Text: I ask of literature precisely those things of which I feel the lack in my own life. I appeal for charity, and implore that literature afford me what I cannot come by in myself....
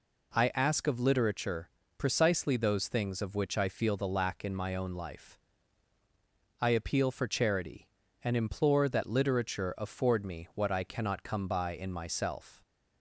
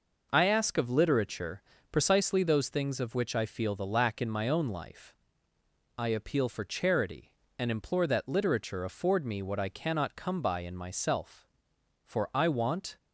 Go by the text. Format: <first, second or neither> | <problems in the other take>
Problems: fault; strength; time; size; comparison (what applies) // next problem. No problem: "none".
first | pauses between "literature" and "precisely"; slight; at 1.6 s; 0.28 s long; slight in the first // goes on to say "For I want"; noticeable; from 12.0 s on; 0.92 s long